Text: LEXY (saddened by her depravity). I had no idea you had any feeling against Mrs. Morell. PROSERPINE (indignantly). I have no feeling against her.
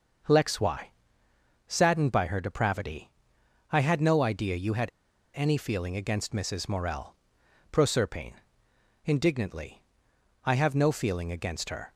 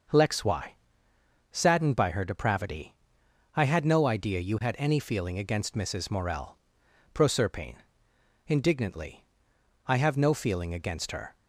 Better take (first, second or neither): second